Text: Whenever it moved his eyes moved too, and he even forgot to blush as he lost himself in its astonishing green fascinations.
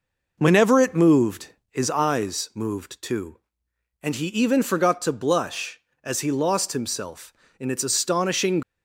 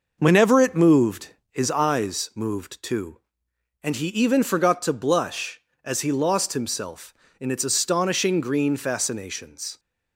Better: second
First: pauses between "moved" and "his"; slight; at 1.4 s; 0.24 s long // stops before "green fascinations"; at 8.6 s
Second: pauses between "moved" and "his"; slight; at 1.2 s; 0.24 s long

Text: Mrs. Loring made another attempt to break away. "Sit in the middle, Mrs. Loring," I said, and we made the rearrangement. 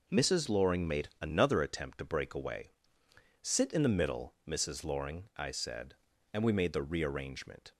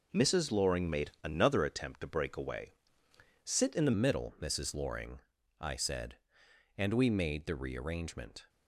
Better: first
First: none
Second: changes voice at "middle"; from 3.9 s on; 4.5 s long

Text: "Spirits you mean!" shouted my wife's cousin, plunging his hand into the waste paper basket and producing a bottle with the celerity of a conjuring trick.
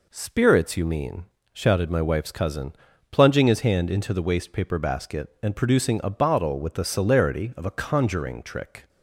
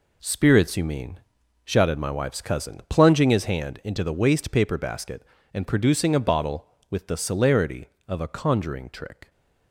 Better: first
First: none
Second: gets quieter; strong; throughout; 8 dB

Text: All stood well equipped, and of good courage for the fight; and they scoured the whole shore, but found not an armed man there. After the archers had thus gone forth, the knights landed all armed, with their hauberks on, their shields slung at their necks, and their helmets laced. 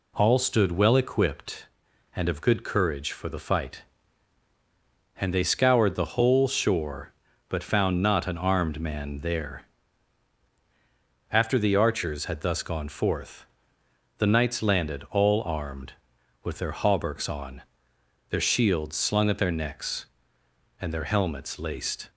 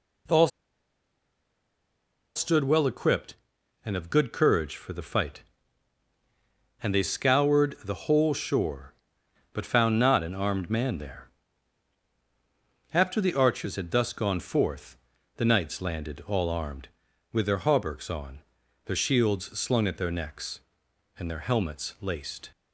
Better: first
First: none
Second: pauses between "All" and "stood"; strong; at 0.4 s; 1.8 s long

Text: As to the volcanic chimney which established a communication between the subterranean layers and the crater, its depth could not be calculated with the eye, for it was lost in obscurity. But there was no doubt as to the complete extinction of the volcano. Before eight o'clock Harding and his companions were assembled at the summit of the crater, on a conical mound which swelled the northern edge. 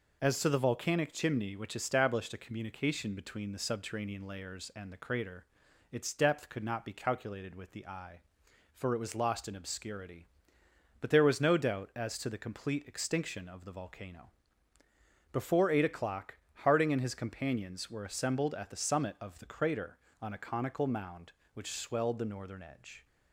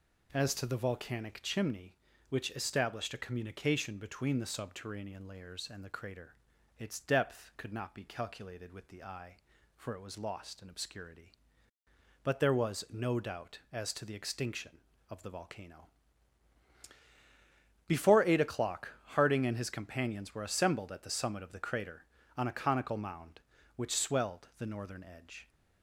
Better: first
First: pauses between "o'clock" and "Harding"; slight; at 16.3 s; 0.28 s long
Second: skips "complete"; at 14.1 s // pauses between "o'clock" and "Harding"; slight; at 18.9 s; 0.24 s long

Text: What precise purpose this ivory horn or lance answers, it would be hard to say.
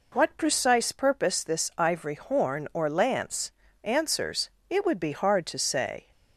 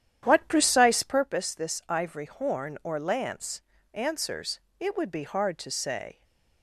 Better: first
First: pauses between "lance" and "answers"; slight; at 3.5 s; 0.32 s long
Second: starts louder than the rest; strong; until 1.2 s; 10.5 dB // pauses between "lance" and "answers"; slight; at 3.6 s; 0.32 s long // stays silent after the last word; slight; from 6.1 s on; 0.5 s long

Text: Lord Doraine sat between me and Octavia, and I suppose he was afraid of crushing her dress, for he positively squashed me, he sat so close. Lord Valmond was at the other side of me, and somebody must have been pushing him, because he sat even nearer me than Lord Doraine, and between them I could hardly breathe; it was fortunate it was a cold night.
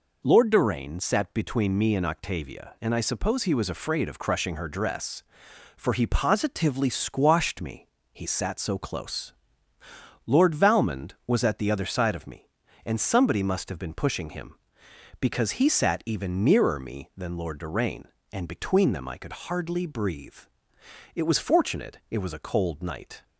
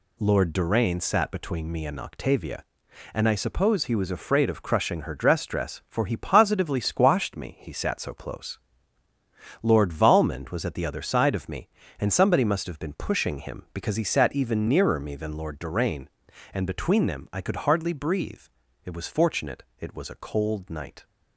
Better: first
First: none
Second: says "dress" twice; at 5.4 s // pauses between "fortunate" and "it"; slight; at 19.6 s; 0.16 s long

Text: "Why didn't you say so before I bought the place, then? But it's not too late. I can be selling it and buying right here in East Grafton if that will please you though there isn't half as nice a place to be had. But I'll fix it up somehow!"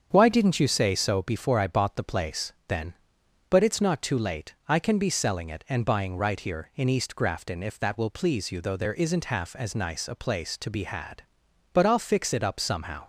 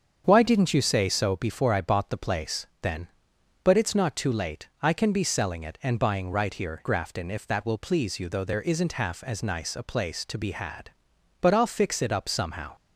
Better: first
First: starts louder than the rest; strong; until 1.1 s; 7 dB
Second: starts louder than the rest; until 1.2 s; 7 dB // skips "in East"; at 6.8 s

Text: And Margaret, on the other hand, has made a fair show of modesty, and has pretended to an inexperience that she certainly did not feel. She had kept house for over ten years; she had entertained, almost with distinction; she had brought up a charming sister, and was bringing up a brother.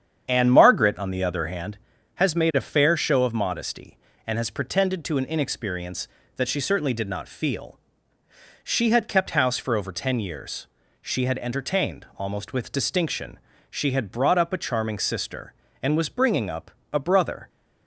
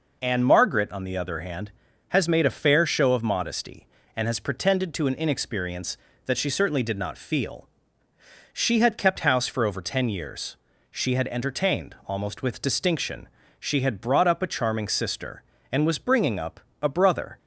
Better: second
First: starts louder than the rest; strong; until 1.7 s; 8 dB // pauses between "up" and "a"; slight; at 16.7 s; 0.20 s long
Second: pauses between "up" and "a"; slight; at 16.6 s; 0.20 s long

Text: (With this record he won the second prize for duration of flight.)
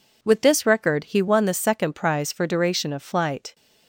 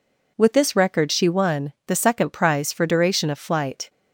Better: first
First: none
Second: says "she" for "he"; at 1.1 s

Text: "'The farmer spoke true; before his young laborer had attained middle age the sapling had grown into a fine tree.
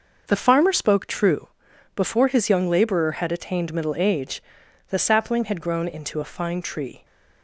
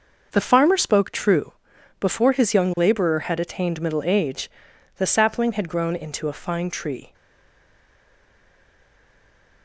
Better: first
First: pauses between "age" and "the"; noticeable; at 4.4 s; 0.48 s long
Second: pauses between "age" and "the"; noticeable; at 4.4 s; 0.48 s long // stays silent after the last word; strong; from 7.1 s on; 2.5 s long

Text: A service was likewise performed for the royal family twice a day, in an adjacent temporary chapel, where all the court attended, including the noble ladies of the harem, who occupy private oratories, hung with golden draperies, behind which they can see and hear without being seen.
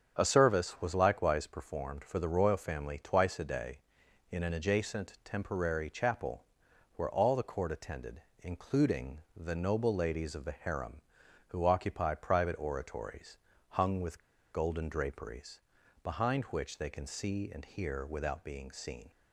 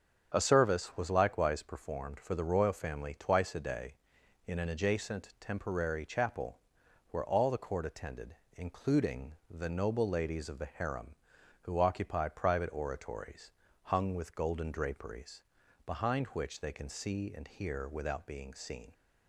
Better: second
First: starts louder than the rest; strong; until 1.1 s; 8 dB // pauses between "including" and "the"; slight; at 9.1 s; 0.16 s long // pauses between "with" and "golden"; slight; at 14.1 s; 0.32 s long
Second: starts louder than the rest; strong; until 1.3 s; 8 dB // pauses between "including" and "the"; slight; at 9.3 s; 0.16 s long

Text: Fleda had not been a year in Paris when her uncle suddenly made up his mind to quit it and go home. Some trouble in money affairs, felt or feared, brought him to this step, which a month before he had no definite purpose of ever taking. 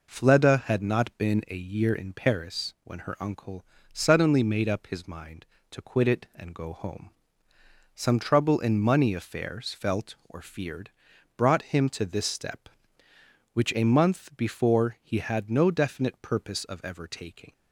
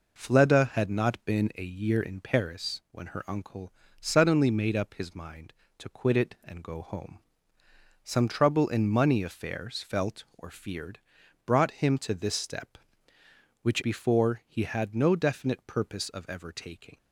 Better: first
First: pauses between "uncle" and "suddenly"; slight; at 3.6 s; 0.30 s long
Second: pauses between "uncle" and "suddenly"; slight; at 3.7 s; 0.30 s long // skips "a month"; at 13.8 s

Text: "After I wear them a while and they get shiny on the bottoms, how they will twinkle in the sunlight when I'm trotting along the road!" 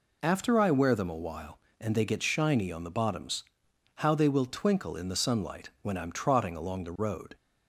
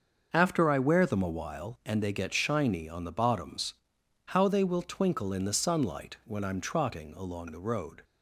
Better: first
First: none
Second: gets quieter; strong; throughout; 9.5 dB

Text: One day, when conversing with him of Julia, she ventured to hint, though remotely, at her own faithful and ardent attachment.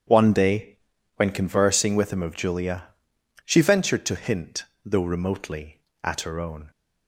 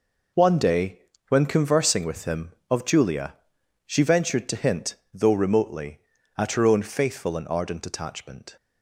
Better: second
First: starts louder than the rest; strong; until 1.4 s; 8.5 dB // stops before "faithful and ardent attachment"; at 6.7 s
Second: none

